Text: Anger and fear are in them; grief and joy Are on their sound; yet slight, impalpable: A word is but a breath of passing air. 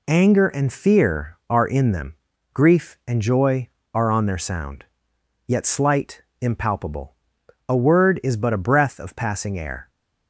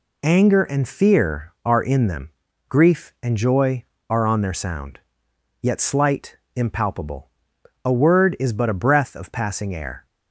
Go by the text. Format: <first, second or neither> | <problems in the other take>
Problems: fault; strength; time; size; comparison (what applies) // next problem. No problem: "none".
neither | none